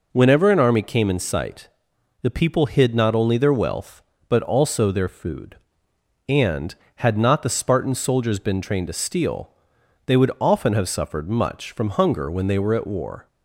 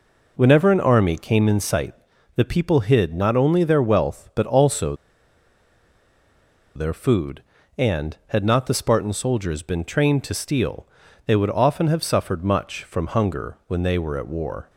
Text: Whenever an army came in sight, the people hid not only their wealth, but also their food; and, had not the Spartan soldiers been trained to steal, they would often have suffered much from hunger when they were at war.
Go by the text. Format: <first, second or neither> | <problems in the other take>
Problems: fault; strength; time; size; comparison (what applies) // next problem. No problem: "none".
first | pauses between "also" and "their"; strong; at 4.9 s; 1.8 s long